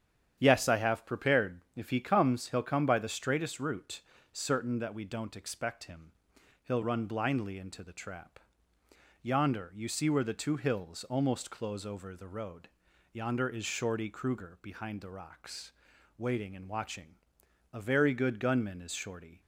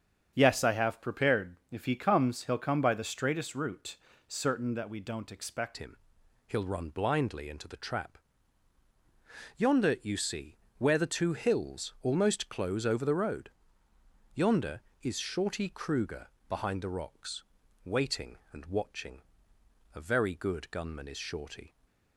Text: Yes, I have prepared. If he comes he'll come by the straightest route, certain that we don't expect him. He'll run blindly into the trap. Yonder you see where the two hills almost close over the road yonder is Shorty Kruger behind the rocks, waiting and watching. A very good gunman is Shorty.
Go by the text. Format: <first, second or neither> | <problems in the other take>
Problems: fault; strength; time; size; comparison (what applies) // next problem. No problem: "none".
first | starts louder than the rest; strong; until 1.3 s; 7.5 dB; strong in the first // changes voice at "him"; from 5.7 s on; 16.0 s long // pauses between "see" and "where"; slight; at 10.5 s; 0.20 s long // pauses between "road" and "yonder"; noticeable; at 13.4 s; 0.86 s long; noticeable in the first // pauses between "Kruger" and "behind"; slight; at 16.2 s; 0.22 s long